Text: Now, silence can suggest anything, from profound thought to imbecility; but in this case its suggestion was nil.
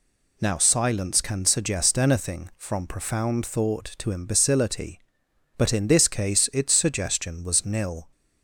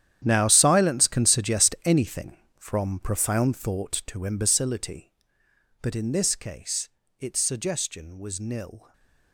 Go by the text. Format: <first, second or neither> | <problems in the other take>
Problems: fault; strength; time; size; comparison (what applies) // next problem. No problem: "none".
first | gets quieter; strong; throughout; 15.5 dB // pauses between "case" and "its"; slight; at 6.8 s; 0.28 s long